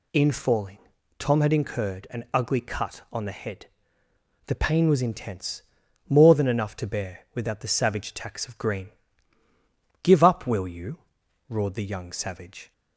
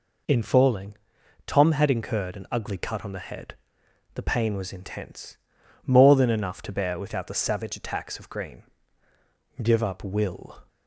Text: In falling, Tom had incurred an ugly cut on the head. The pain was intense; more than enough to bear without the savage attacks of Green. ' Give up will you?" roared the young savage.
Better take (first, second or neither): first